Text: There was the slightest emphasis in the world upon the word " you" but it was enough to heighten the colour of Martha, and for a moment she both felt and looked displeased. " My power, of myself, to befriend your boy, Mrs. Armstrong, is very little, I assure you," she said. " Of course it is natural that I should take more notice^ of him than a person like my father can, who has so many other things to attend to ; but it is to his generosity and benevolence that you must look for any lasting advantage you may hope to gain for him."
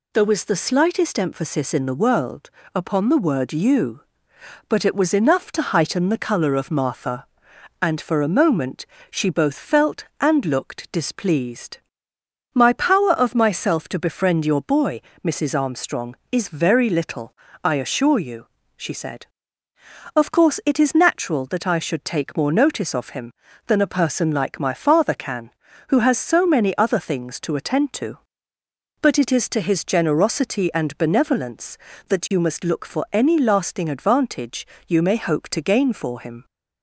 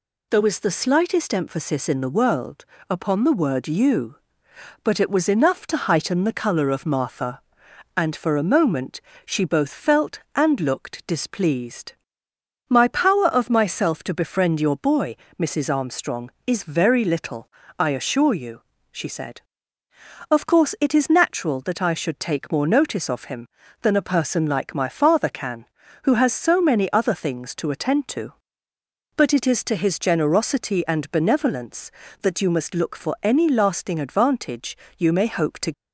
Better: first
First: pauses between "world" and "upon"; slight; at 2.4 s; 0.24 s long // pauses between "moment" and "she"; slight; at 8.8 s; 0.24 s long // pauses between "advantage" and "you"; slight; at 34.6 s; 0.20 s long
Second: pauses between "world" and "upon"; slight; at 2.6 s; 0.24 s long // pauses between "moment" and "she"; slight; at 9.0 s; 0.24 s long // pauses between "advantage" and "you"; slight; at 34.7 s; 0.20 s long // stops before "gain for him"; at 35.7 s

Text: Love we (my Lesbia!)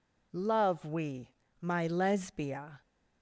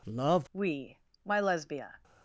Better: first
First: none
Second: changes voice at "we"; from 0.5 s on; 1.4 s long

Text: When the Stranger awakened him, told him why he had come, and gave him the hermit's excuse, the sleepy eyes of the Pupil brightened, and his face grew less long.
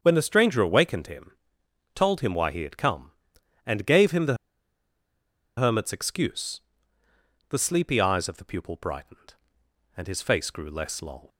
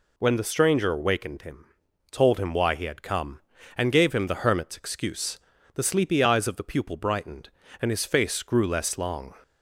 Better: second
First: starts louder than the rest; until 1.0 s; 7 dB // pauses between "the" and "hermit's"; at 4.3 s; 1.2 s long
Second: none

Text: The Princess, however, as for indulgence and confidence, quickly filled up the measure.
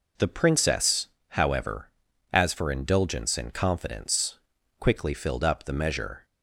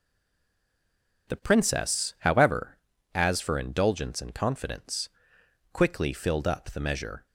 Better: first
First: none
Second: stays silent before the first word; noticeable; until 1.2 s; 1.2 s long

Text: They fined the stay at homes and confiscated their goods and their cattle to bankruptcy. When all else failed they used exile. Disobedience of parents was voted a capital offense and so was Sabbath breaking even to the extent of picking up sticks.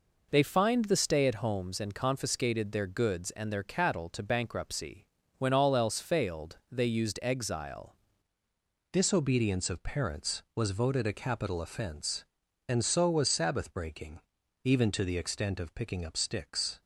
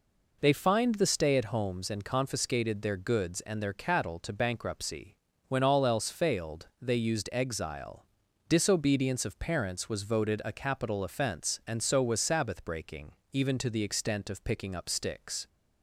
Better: second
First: changes voice at "Disobedience"; from 8.9 s on; 7.9 s long // pauses between "breaking" and "even"; at 14.2 s; 0.42 s long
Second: pauses between "breaking" and "even"; slight; at 13.1 s; 0.20 s long

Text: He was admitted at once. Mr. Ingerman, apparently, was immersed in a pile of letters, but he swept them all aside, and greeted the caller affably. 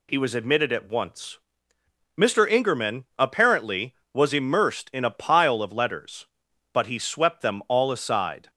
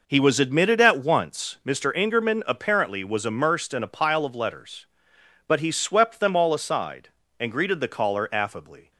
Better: second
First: stops before "and greeted the caller affably"; at 8.4 s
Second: none

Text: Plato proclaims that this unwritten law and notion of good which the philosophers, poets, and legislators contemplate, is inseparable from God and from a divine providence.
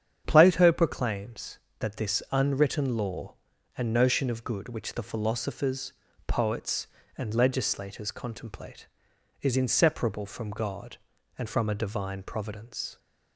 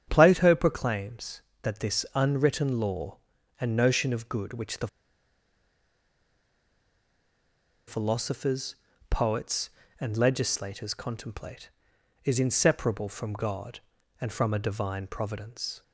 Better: first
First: starts louder than the rest; strong; until 1.2 s; 8.5 dB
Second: starts louder than the rest; strong; until 1.0 s; 8.5 dB // pauses between "the" and "philosophers"; strong; at 4.8 s; 3.0 s long

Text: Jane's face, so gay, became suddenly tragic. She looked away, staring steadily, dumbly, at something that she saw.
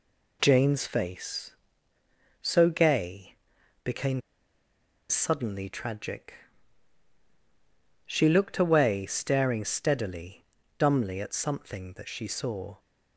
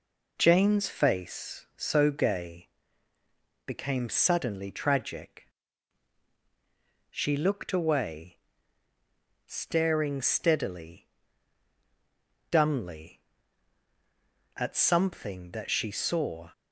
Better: second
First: pauses between "became" and "suddenly"; noticeable; at 4.2 s; 0.88 s long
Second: none

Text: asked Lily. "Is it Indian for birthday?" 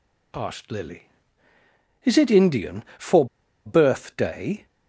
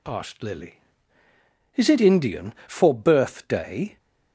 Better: second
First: pauses between "for" and "birthday"; at 3.2 s; 0.39 s long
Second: none

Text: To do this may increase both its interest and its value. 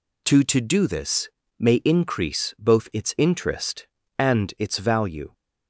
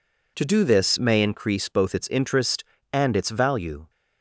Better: second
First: says "To" twice; at 0.4 s // pauses between "this" and "may"; slight; at 1.2 s; 0.30 s long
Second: none

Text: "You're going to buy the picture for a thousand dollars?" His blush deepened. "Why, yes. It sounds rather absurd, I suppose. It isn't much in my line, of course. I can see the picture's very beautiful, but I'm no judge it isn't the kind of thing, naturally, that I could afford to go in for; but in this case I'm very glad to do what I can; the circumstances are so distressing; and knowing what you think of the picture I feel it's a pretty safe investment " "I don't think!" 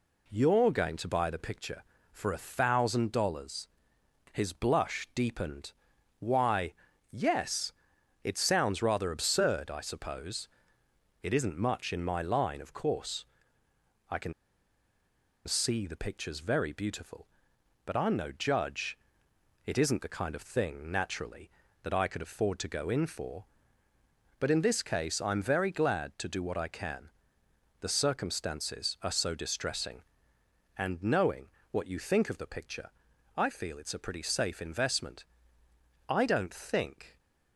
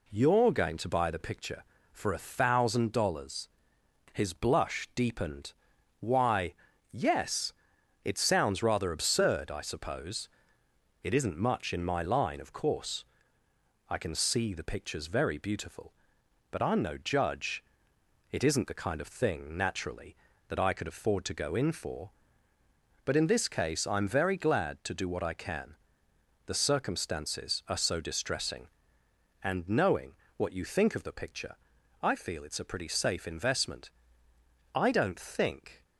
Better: second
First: pauses between "can" and "see"; at 14.3 s; 1.1 s long // pauses between "judge" and "it"; noticeable; at 18.9 s; 0.68 s long // pauses between "knowing" and "what"; slight; at 31.4 s; 0.22 s long // pauses between "picture" and "I"; at 32.9 s; 0.44 s long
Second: pauses between "judge" and "it"; noticeable; at 17.6 s; 0.68 s long // pauses between "knowing" and "what"; slight; at 30.1 s; 0.22 s long // pauses between "picture" and "I"; at 31.5 s; 0.44 s long

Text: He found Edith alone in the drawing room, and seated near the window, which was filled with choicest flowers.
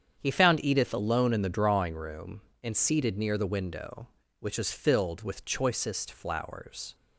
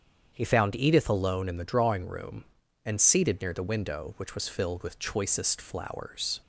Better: neither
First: starts louder than the rest; strong; until 1.1 s; 8 dB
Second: starts louder than the rest; strong; until 1.3 s; 8 dB

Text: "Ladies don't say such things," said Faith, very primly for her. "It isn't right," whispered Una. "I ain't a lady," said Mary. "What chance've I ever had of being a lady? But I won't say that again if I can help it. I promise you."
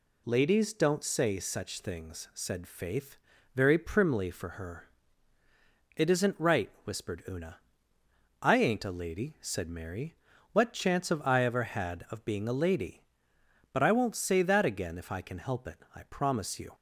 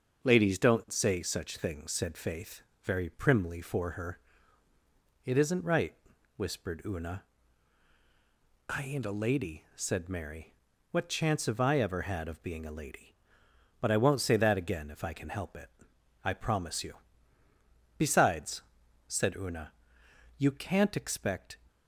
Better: first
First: none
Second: starts louder than the rest; until 1.2 s; 6.5 dB // goes on to say "Besides said Una you can't expect"; strong; from 17.9 s on; 3.6 s long

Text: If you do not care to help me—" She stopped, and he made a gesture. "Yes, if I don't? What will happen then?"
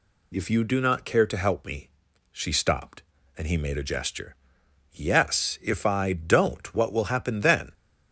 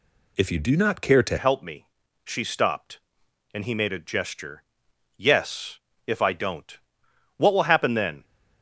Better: first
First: none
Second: changes voice at "help"; from 1.3 s on; 6.9 s long

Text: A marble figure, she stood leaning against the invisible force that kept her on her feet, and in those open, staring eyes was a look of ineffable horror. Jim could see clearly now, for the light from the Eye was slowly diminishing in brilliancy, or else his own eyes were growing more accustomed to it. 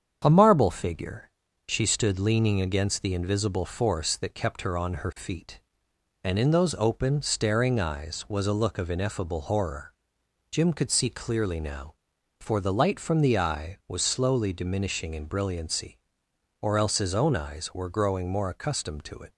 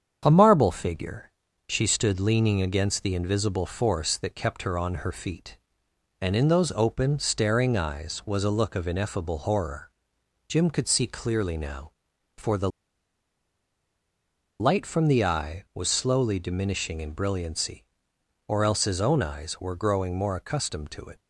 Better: first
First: starts louder than the rest; strong; until 1.2 s; 8 dB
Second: starts louder than the rest; strong; until 1.2 s; 8 dB // pauses between "the" and "light"; strong; at 12.6 s; 1.9 s long

